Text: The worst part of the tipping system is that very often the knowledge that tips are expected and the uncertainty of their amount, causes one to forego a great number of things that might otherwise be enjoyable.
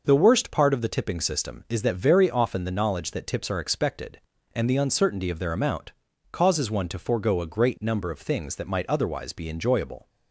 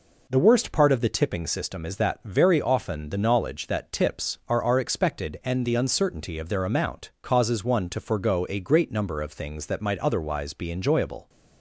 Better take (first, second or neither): first